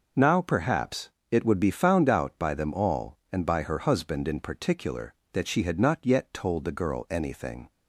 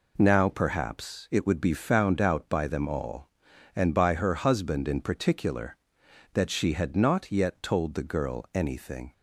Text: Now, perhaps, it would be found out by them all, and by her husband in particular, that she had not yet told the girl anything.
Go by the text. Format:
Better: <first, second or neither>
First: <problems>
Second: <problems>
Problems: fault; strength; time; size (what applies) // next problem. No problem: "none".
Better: neither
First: none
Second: none